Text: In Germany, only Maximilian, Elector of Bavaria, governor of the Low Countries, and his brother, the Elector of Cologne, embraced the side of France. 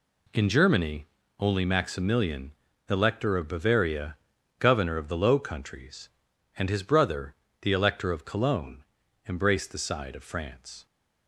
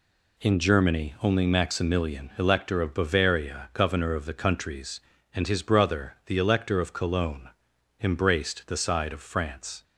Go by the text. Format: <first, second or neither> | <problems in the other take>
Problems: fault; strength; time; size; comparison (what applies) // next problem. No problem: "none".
first | skips "Low"; at 4.3 s